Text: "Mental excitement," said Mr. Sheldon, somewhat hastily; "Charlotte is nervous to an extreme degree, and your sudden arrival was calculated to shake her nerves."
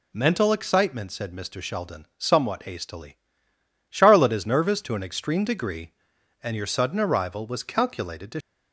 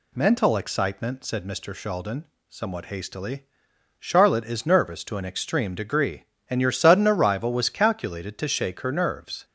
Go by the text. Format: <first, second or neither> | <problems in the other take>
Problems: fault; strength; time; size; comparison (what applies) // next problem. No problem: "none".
second | stops before "shake her nerves"; at 8.4 s